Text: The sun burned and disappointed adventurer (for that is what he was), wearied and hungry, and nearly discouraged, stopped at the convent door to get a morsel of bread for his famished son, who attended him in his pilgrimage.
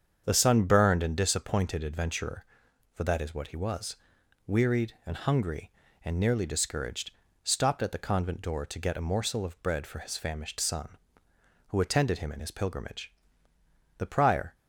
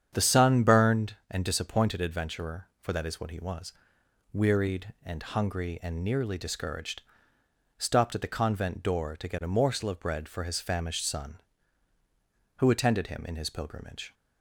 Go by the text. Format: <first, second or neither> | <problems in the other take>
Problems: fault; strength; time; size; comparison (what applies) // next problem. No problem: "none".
second | starts louder than the rest; strong; until 1.2 s; 7.5 dB; strong in the second // goes on to say "The prior"; from 13.9 s on; 0.58 s long